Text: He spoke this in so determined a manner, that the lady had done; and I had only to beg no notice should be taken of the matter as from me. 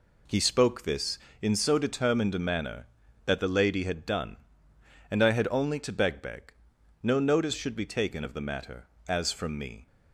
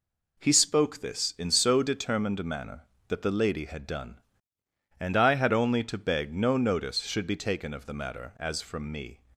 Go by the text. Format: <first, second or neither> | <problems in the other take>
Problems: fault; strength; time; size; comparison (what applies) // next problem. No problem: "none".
second | says "beg" twice; at 6.1 s